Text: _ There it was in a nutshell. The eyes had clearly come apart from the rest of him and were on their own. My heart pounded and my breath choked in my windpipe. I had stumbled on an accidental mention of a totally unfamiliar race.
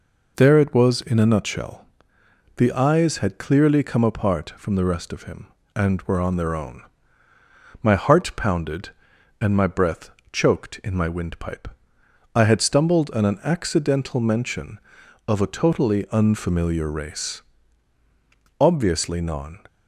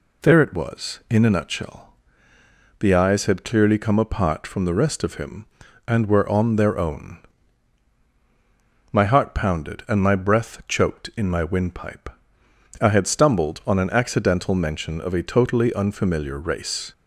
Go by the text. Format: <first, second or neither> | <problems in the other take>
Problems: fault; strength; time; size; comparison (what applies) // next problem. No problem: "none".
second | pauses between "breath" and "choked"; slight; at 10.1 s; 0.22 s long // goes on to say "Obviously non"; noticeable; from 18.5 s on; 1.0 s long